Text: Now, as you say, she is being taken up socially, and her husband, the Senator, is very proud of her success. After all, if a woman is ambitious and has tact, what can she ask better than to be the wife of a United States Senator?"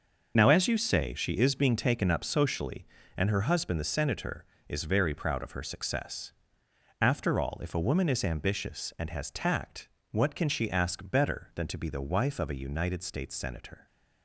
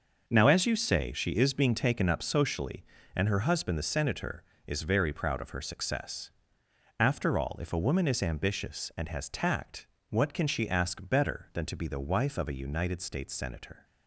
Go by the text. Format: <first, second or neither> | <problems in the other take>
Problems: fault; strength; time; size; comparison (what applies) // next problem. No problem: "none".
second | loses the start of "Now"; at 0.3 s; 50 ms